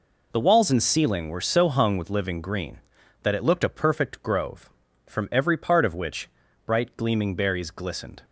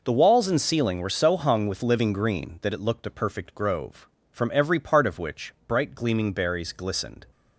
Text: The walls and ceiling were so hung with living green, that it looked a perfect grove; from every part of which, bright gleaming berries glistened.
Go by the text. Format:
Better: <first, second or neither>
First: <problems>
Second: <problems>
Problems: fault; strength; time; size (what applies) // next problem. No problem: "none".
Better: neither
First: none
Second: none